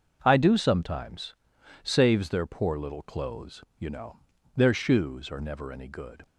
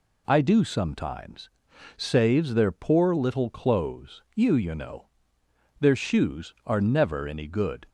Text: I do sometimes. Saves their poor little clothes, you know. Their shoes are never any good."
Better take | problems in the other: first | says "you" twice; at 4.5 s

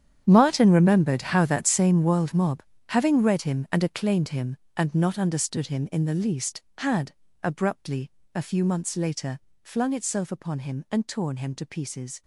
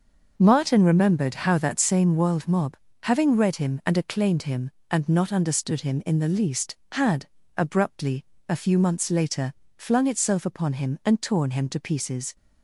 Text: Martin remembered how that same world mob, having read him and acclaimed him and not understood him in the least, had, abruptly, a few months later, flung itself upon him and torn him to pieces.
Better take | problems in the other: second | gets quieter; strong; throughout; 16 dB // starts louder than the rest; strong; until 1.2 s; 9.5 dB; noticeable in the second

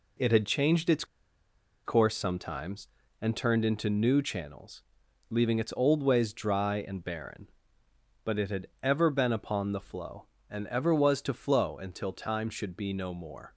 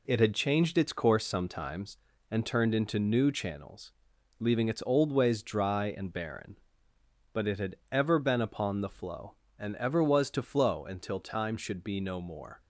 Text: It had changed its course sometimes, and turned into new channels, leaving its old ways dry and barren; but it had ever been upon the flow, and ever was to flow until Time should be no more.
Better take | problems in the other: second | pauses between "its" and "course"; noticeable; at 1.0 s; 0.81 s long // pauses between "had" and "ever"; slight; at 8.6 s; 0.16 s long; slight in the second

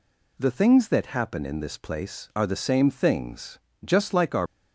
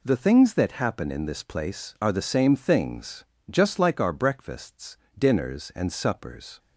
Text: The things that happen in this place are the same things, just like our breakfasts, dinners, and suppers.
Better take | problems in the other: second | stops before "breakfasts dinners and suppers"; at 4.4 s

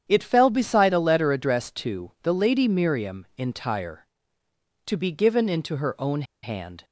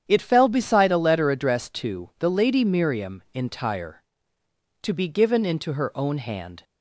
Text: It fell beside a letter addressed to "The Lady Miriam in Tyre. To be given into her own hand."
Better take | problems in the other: second | starts louder than the rest; strong; until 1.0 s; 9 dB; strong in the second // pauses between "own" and "hand"; slight; at 6.2 s; 0.20 s long

